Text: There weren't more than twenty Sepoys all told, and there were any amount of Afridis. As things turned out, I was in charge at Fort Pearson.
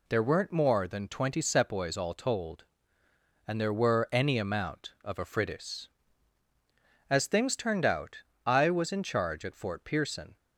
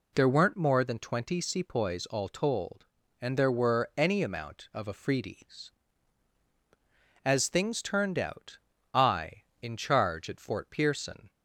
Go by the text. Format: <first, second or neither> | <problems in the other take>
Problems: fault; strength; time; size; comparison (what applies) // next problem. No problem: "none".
first | skips "was"; at 9.5 s